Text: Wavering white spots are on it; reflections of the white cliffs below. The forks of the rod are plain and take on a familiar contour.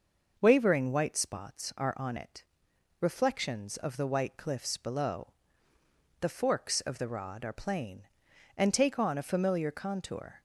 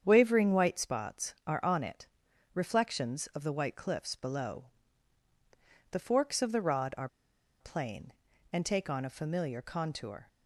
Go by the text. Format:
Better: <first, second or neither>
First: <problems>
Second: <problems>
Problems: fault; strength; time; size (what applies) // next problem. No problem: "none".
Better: first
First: none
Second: starts louder than the rest; strong; until 1.0 s; 8 dB // pauses between "are" and "plain"; noticeable; at 7.0 s; 0.53 s long